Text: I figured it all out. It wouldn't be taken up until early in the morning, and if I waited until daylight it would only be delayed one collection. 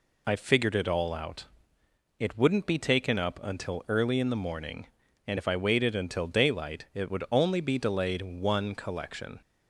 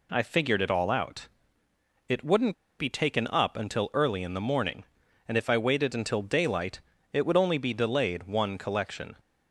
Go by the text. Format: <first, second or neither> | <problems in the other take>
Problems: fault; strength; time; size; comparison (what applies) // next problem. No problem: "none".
first | pauses between "wouldn't" and "be"; slight; at 2.5 s; 0.25 s long // pauses between "daylight" and "it"; slight; at 6.8 s; 0.32 s long